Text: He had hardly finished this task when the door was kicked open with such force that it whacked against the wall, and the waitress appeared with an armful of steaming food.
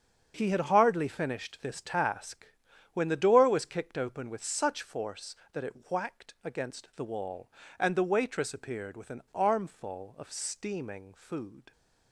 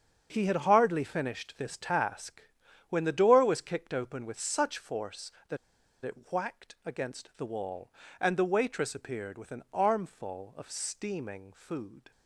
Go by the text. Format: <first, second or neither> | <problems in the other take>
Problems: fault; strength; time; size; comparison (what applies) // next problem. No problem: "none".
first | starts louder than the rest; until 1.3 s; 6.5 dB; also in the first // pauses between "task" and "when"; noticeable; at 2.4 s; 0.48 s long; noticeable in the first // pauses between "that" and "it"; noticeable; at 5.5 s; 0.47 s long